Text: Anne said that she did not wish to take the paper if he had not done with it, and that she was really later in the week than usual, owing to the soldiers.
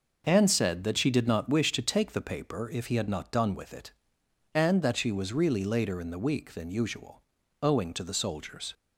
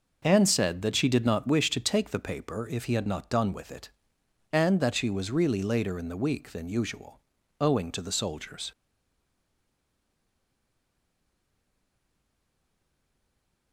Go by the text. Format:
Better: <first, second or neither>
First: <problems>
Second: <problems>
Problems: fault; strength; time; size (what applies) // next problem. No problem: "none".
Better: first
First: none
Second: stays silent after the last word; strong; from 8.7 s on; 5.0 s long